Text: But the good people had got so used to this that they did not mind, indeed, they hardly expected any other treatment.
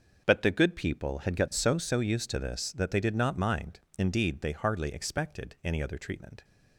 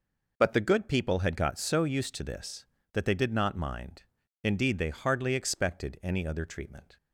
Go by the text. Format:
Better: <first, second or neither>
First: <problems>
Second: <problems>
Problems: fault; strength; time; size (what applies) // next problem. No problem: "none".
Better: second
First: starts louder than the rest; until 1.2 s; 6.5 dB // says "so" twice; at 1.7 s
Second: none